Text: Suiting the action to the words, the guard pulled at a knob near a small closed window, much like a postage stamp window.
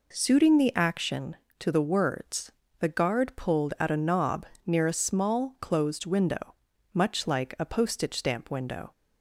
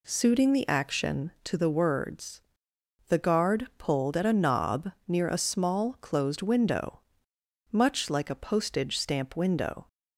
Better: neither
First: pauses between "knob" and "near"; slight; at 4.4 s; 0.20 s long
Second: pauses between "knob" and "near"; slight; at 4.9 s; 0.16 s long

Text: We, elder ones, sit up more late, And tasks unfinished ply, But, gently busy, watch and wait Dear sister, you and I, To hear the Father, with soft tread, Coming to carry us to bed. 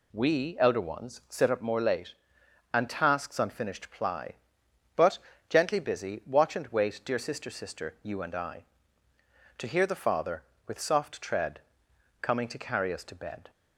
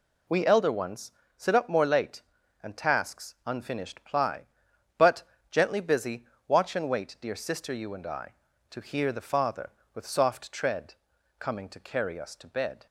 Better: second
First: says "sister" twice; at 7.4 s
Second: none

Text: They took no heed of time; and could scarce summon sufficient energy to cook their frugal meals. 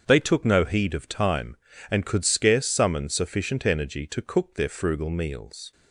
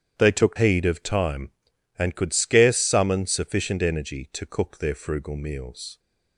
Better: first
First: starts louder than the rest; strong; until 1.0 s; 7 dB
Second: starts louder than the rest; strong; until 1.1 s; 9.5 dB // skips "no"; at 0.5 s

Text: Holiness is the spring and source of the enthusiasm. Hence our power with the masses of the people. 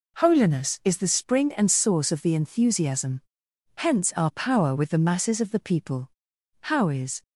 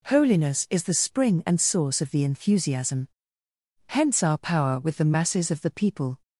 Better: second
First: goes on to say "How is"; from 6.6 s on; 0.60 s long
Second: none

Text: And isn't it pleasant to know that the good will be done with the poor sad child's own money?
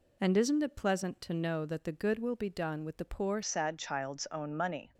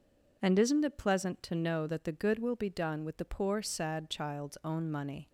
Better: second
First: changes voice at "sad"; from 3.4 s on; 1.5 s long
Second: none

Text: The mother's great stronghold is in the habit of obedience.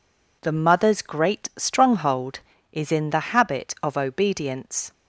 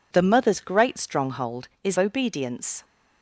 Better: first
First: none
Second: skips "in the habit of"; at 1.9 s

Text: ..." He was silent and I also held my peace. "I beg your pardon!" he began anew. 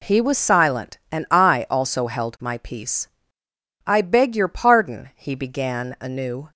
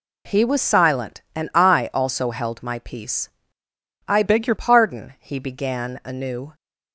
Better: first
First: none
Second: changes voice from "beg" to "your"; from 4.2 to 4.5 s; 0.3 s long

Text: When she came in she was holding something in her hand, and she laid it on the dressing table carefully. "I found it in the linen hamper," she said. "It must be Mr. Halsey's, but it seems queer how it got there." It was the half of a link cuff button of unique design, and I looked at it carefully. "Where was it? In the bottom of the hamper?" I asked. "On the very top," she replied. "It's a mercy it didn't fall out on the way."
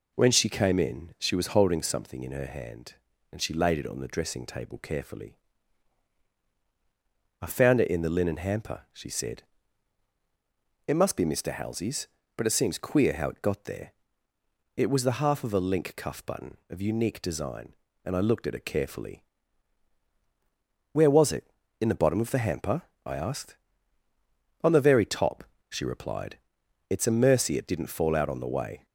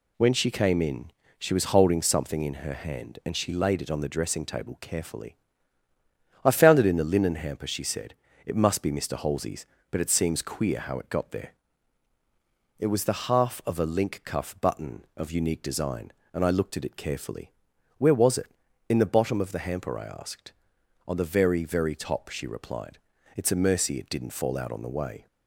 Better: first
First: none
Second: pauses between "in" and "she"; slight; at 1.1 s; 0.30 s long // says "very" twice; at 21.6 s

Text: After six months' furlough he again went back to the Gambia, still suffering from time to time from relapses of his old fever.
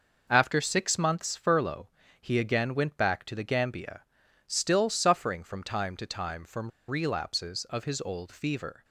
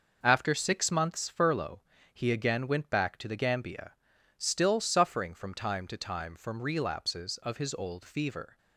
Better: second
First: pauses between "furlough" and "he"; slight; at 1.8 s; 0.32 s long // pauses between "from" and "relapses"; slight; at 6.7 s; 0.19 s long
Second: pauses between "furlough" and "he"; slight; at 1.8 s; 0.32 s long

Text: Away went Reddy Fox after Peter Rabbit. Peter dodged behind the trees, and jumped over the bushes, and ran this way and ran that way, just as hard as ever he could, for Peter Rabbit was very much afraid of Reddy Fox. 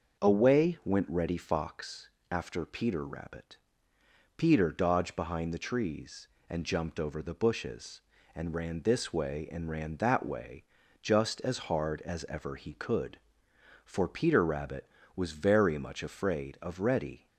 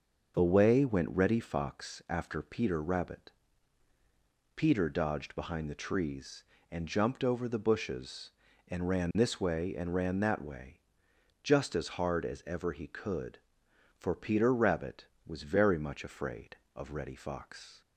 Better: second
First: starts louder than the rest; noticeable; until 1.2 s; 6 dB // pauses between "Fox" and "after"; slight; at 2.0 s; 0.24 s long // stops before "Fox"; at 17.2 s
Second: none

